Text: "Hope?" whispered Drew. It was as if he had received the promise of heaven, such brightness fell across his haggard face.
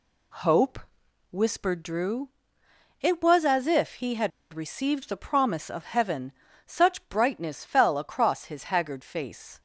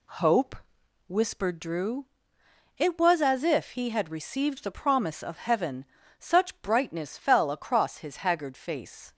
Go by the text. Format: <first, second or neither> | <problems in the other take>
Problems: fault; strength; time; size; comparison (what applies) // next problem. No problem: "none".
second | pauses between "had" and "received"; slight; at 4.3 s; 0.22 s long